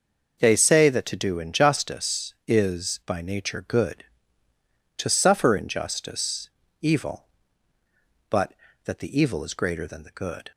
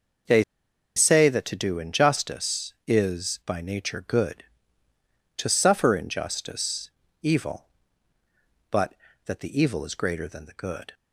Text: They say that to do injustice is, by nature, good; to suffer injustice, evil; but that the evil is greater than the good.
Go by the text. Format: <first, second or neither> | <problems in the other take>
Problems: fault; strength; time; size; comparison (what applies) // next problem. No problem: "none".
first | pauses between "They" and "say"; noticeable; at 0.4 s; 0.54 s long